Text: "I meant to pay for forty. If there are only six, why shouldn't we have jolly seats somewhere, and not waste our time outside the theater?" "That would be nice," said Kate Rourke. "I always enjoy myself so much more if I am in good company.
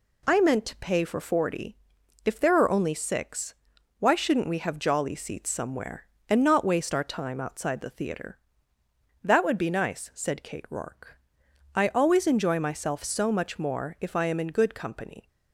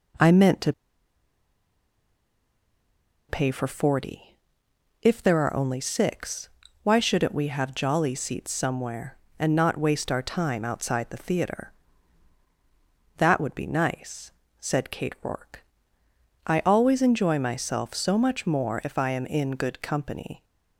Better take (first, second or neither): first